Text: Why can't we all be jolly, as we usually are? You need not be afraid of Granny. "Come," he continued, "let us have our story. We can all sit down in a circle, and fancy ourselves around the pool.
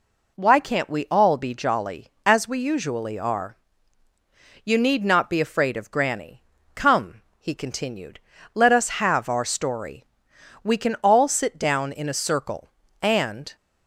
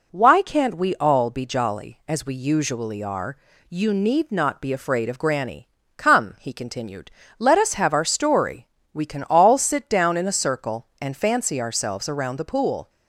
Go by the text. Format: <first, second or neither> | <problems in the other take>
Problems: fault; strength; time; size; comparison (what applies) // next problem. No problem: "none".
second | stops before "fancy ourselves around the pool"; at 13.5 s